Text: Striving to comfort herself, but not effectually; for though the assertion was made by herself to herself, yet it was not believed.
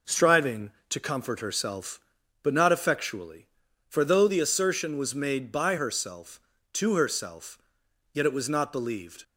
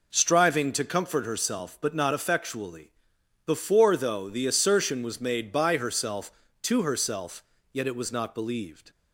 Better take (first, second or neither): first